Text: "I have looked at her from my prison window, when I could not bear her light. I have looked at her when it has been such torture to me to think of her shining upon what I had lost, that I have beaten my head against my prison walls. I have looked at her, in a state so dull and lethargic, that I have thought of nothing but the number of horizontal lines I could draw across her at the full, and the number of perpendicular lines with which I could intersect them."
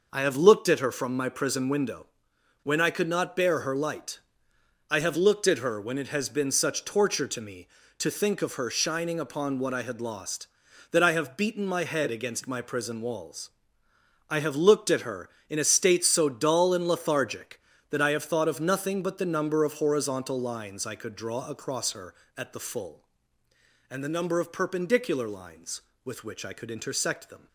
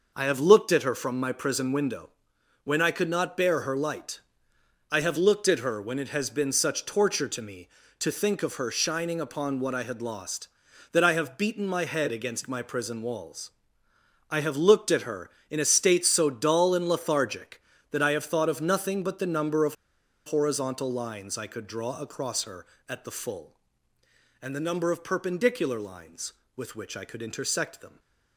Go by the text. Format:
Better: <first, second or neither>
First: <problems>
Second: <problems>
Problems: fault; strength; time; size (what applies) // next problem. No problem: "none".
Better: first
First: none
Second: pauses between "of" and "horizontal"; noticeable; at 19.7 s; 0.51 s long